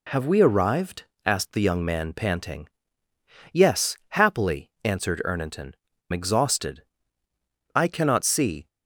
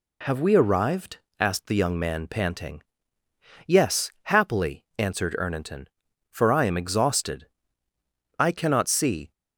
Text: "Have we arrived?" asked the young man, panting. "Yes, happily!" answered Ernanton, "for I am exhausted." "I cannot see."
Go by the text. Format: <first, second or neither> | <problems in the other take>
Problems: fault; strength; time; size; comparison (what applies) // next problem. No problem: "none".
second | skips "for I am"; at 5.9 s